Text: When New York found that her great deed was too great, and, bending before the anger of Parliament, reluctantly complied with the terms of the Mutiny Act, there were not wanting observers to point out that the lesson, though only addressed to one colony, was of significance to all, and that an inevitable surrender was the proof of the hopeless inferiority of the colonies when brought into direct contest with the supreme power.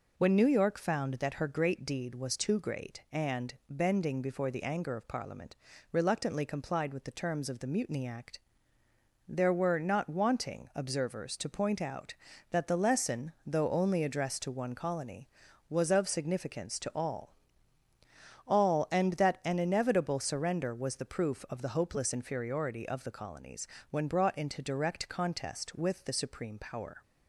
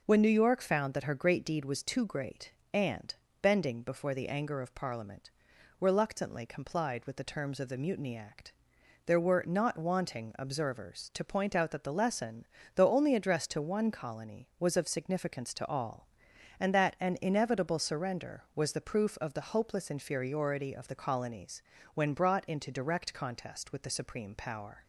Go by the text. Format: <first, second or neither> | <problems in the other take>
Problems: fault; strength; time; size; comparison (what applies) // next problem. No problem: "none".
second | says "all" twice; at 18.4 s // pauses between "colonies" and "when"; slight; at 23.6 s; 0.24 s long; slight in the second